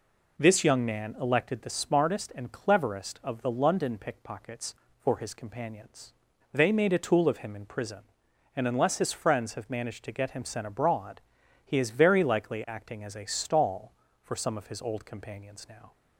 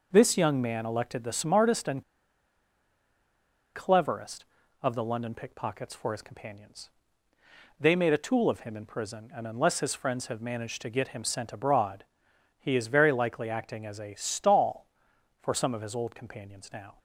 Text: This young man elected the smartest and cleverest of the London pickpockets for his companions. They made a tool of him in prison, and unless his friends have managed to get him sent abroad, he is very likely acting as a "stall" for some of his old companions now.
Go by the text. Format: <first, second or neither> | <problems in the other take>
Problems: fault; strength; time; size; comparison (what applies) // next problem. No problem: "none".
first | pauses between "and" and "cleverest"; strong; at 2.0 s; 1.7 s long